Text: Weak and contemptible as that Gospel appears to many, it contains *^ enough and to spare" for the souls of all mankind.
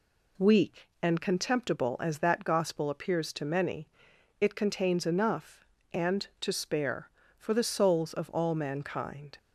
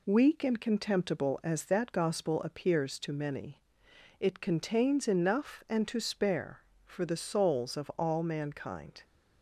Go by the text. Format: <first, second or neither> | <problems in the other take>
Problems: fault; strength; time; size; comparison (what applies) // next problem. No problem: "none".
neither | none